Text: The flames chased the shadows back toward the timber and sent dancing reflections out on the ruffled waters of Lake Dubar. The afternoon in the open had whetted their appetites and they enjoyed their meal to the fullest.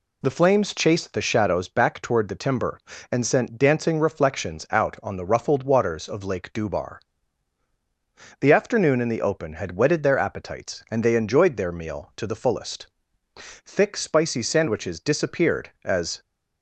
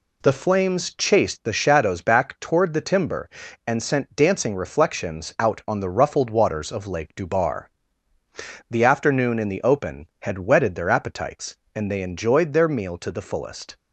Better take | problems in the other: second | goes on to say "Thick spicy sandwiches disappeared as"; strong; from 13.3 s on; 2.8 s long

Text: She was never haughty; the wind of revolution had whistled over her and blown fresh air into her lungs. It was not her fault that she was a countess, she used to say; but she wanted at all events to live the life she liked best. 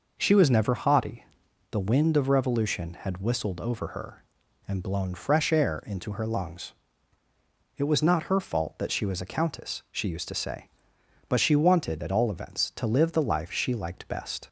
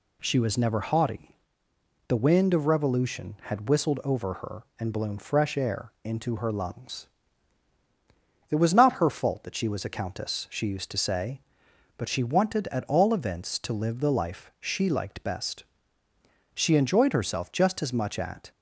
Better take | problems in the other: first | goes on to say "She enjoyed herself just as much at"; strong; from 16.5 s on; 1.9 s long

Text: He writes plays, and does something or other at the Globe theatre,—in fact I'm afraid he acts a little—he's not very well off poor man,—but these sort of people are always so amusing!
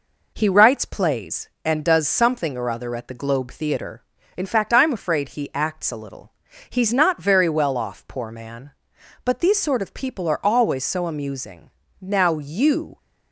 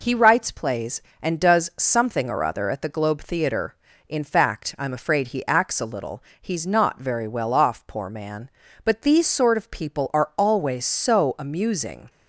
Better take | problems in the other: second | goes on to say "Now you"; noticeable; from 12.0 s on; 0.96 s long

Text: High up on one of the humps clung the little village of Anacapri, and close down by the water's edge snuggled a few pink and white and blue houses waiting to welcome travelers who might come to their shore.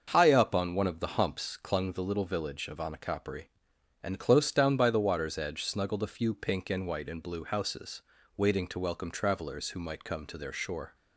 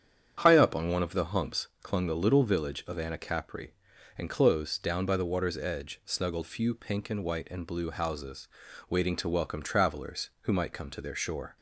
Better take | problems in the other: first | starts louder than the rest; strong; until 1.4 s; 8.5 dB; also in the first // pauses between "humps" and "clung"; slight; at 1.6 s; 0.16 s long // skips "a"; at 6.4 s // pauses between "houses" and "waiting"; at 8.4 s; 0.42 s long; slight in the first

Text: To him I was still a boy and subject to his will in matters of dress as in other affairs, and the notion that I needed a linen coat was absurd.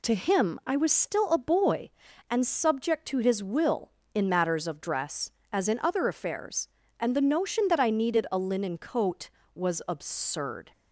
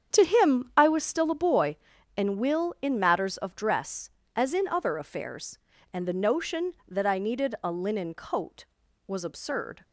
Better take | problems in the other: first | starts louder than the rest; strong; until 1.1 s; 8 dB // skips "subject to his"; at 2.3 s

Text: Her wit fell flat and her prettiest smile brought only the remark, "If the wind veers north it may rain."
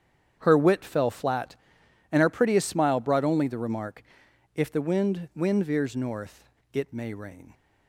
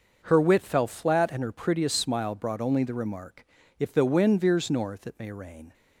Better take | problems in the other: second | starts louder than the rest; strong; until 1.4 s; 8.5 dB // says "wind" twice; at 5.3 s // pauses between "north" and "it"; slight; at 6.4 s; 0.24 s long

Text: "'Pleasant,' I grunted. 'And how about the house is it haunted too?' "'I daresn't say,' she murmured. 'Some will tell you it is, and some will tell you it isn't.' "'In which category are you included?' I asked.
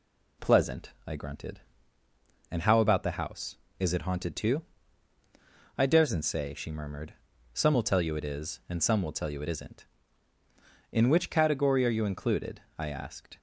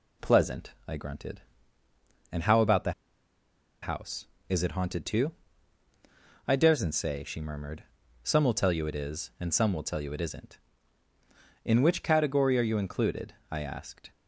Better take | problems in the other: first | pauses between "the" and "house"; noticeable; at 2.9 s; 0.90 s long

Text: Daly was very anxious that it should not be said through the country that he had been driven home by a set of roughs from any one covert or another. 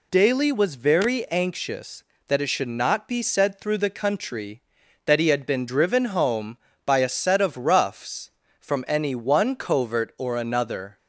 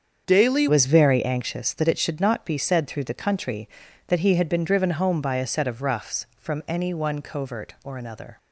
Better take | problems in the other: first | starts louder than the rest; strong; until 1.2 s; 7 dB // changes voice at "was"; from 0.6 s on; 7.7 s long

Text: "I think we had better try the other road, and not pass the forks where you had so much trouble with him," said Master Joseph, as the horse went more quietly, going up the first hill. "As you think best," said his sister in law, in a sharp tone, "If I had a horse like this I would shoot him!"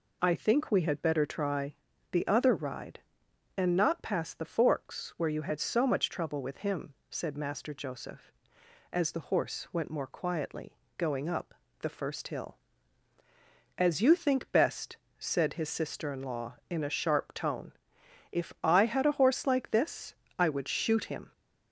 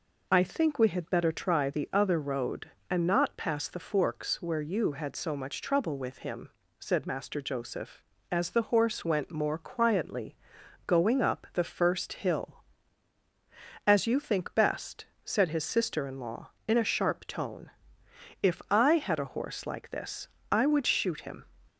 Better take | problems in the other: second | pauses between "try" and "the"; slight; at 1.7 s; 0.36 s long // says "ride" for "road"; at 2.5 s // pauses between "up" and "the"; slight; at 11.5 s; 0.26 s long // pauses between "this" and "I"; slight; at 20.1 s; 0.22 s long; slight in the second

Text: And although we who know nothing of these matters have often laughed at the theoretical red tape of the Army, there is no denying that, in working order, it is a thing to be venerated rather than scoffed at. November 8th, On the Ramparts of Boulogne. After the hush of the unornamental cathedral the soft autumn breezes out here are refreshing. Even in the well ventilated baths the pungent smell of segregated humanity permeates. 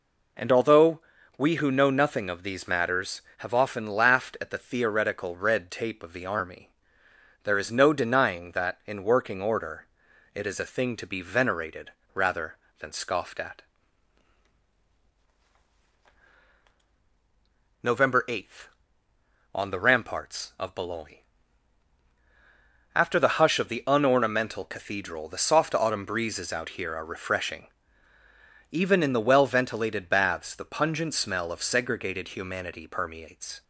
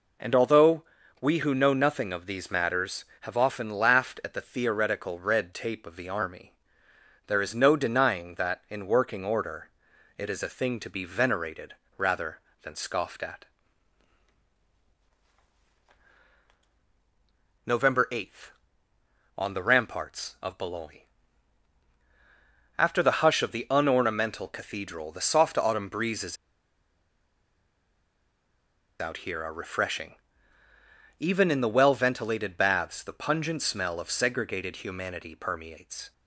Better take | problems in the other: first | pauses between "although" and "we"; at 0.8 s; 0.38 s long; also in the first // pauses between "venerated" and "rather"; slight; at 11.7 s; 0.22 s long; slight in the first // pauses between "breezes" and "out"; strong; at 26.3 s; 2.6 s long

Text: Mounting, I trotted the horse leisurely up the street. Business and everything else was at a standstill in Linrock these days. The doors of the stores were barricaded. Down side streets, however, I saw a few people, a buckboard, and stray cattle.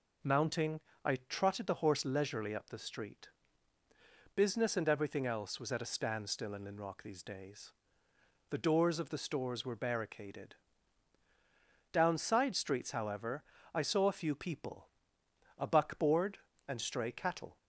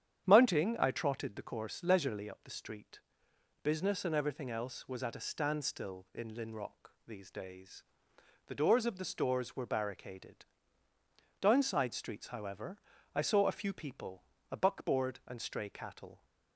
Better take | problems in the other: first | starts louder than the rest; strong; until 1.3 s; 9 dB // says "course" for "horse"; at 1.4 s // pauses between "Linrock" and "these"; slight; at 6.8 s; 0.18 s long

